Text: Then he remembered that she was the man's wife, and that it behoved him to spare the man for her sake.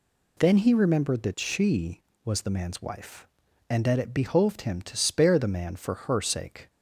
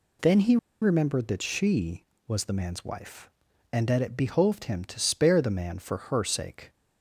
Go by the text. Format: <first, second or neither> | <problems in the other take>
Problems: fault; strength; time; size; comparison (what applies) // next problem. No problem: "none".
first | pauses between "he" and "remembered"; slight; at 0.5 s; 0.25 s long